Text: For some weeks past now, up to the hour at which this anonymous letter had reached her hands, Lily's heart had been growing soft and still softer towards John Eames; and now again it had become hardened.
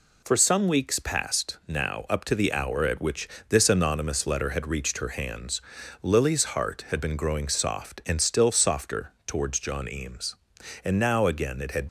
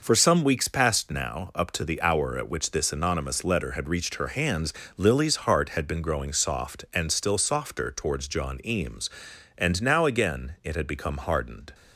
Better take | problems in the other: second | pauses between "which" and "this"; slight; at 3.2 s; 0.22 s long // pauses between "softer" and "towards"; slight; at 9.1 s; 0.16 s long // stops before "become hardened"; at 11.8 s

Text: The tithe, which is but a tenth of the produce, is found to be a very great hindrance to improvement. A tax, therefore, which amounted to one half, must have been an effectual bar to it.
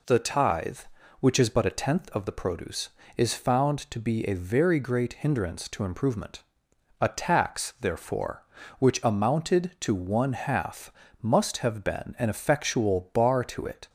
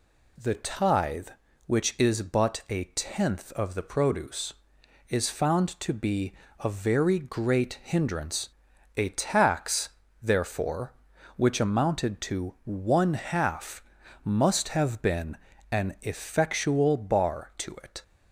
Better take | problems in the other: first | pauses between "be" and "a"; slight; at 6.3 s; 0.28 s long // skips "to improvement"; at 8.7 s // pauses between "been" and "an"; slight; at 15.3 s; 0.36 s long

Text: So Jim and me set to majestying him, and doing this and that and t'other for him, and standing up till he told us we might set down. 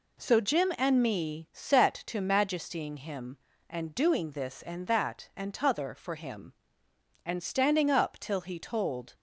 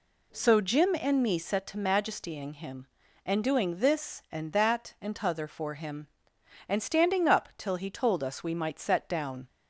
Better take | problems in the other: second | stops before "us we might set down"; at 9.1 s

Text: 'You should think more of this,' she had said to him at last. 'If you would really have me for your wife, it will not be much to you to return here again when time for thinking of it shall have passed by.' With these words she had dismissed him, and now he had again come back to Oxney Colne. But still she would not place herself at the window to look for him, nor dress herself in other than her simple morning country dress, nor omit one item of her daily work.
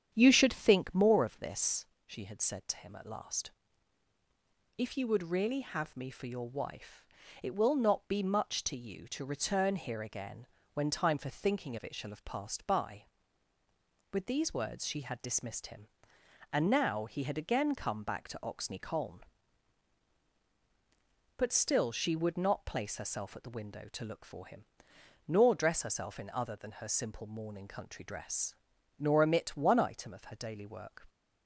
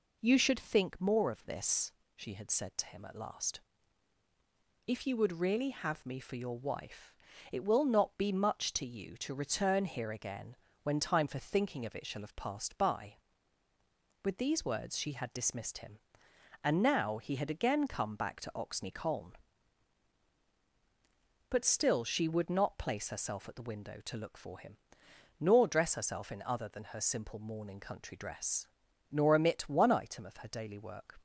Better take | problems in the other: second | starts louder than the rest; strong; until 1.5 s; 8.5 dB // pauses between "again" and "when"; slight; at 10.4 s; 0.28 s long; slight in the second

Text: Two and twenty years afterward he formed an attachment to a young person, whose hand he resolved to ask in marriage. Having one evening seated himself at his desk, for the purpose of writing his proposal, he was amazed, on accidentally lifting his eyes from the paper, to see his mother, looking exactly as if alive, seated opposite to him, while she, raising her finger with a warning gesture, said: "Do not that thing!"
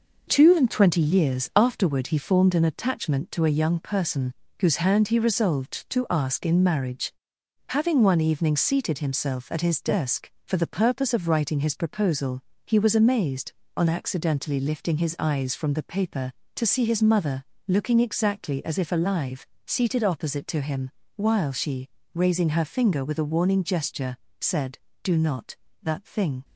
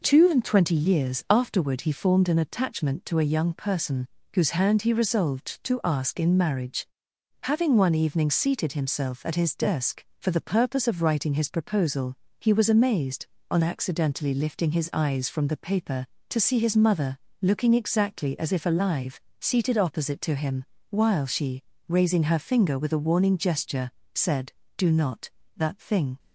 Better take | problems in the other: second | gets quieter; noticeable; throughout; 5 dB

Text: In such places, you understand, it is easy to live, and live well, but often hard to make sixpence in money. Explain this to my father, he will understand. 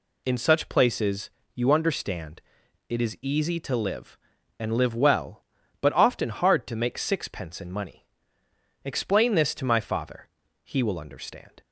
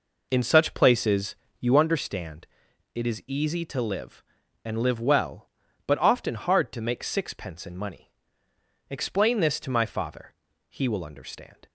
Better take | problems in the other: first | starts louder than the rest; noticeable; until 2.0 s; 4.5 dB

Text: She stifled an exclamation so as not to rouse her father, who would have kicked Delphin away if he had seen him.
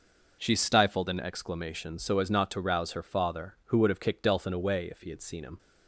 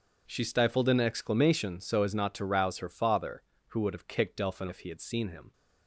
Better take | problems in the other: first | skips "away"; at 4.6 s

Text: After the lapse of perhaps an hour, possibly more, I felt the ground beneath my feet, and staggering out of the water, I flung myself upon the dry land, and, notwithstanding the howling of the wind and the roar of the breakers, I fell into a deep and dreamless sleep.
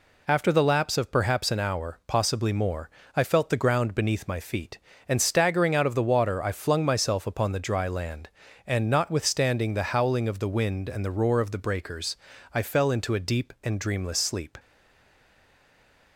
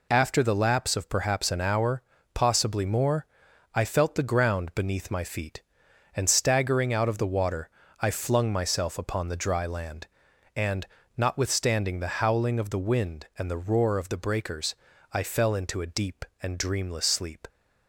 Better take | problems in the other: second | stays silent after the last word; noticeable; from 14.5 s on; 1.6 s long

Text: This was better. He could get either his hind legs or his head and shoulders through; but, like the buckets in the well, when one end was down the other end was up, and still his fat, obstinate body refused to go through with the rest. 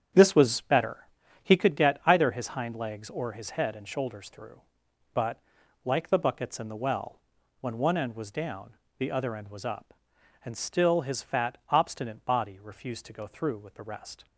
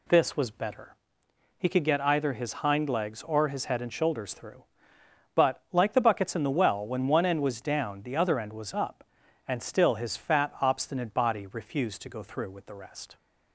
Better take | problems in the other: second | starts louder than the rest; strong; until 1.7 s; 8.5 dB // pauses between "down" and "the"; slight; at 8.7 s; 0.22 s long

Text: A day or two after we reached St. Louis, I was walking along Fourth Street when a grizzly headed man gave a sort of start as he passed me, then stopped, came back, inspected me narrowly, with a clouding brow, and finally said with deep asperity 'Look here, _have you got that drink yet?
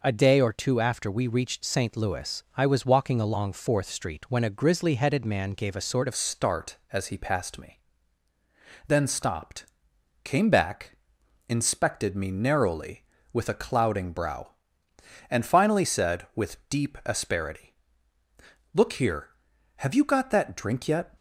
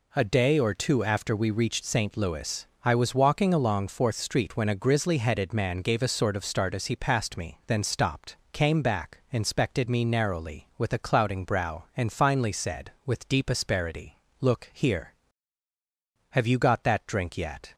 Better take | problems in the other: second | changes voice at "start"; from 6.1 s on; 15.0 s long // pauses between "asperity" and "Look"; noticeable; at 17.7 s; 0.98 s long; slight in the second

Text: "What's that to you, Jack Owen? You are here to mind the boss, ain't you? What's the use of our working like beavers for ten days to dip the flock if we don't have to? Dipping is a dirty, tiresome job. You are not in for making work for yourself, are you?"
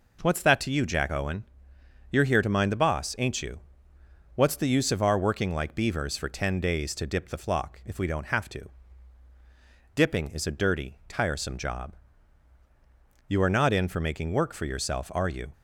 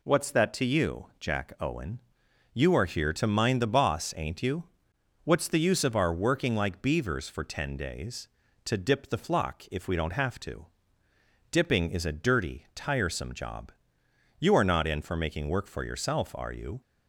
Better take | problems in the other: neither | none

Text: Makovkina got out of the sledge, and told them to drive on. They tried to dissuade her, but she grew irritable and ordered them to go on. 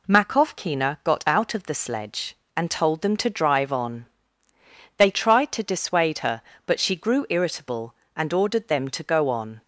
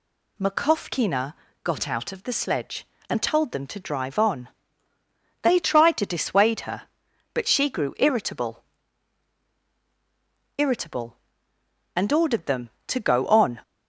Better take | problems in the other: first | pauses between "Makovkina" and "got"; slight; at 1.3 s; 0.32 s long // says "irritable" twice; at 10.5 s

